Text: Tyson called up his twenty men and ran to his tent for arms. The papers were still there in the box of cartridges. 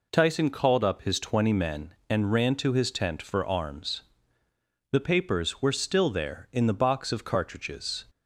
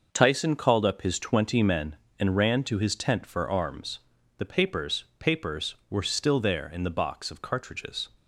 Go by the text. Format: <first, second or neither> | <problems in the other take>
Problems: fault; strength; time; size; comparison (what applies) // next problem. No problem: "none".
first | says "papers" twice; at 5.1 s